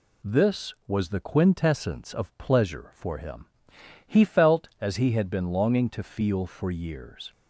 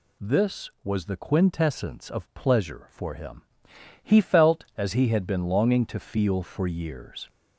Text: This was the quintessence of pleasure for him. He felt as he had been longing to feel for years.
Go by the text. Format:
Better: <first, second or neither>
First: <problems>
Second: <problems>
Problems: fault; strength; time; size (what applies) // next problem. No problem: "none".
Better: first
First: none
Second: gets louder; slight; throughout; 2 dB